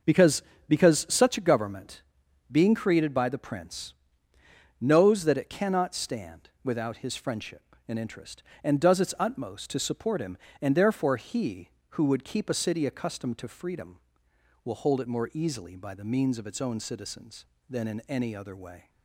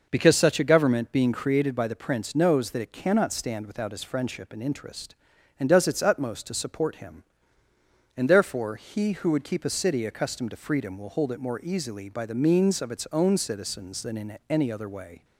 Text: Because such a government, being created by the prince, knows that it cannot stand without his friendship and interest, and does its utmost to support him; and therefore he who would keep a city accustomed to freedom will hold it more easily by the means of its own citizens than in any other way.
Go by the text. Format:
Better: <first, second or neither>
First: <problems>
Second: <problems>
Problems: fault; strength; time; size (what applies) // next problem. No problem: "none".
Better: second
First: starts louder than the rest; noticeable; until 1.3 s; 6 dB // says "Because" twice; at 0.6 s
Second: none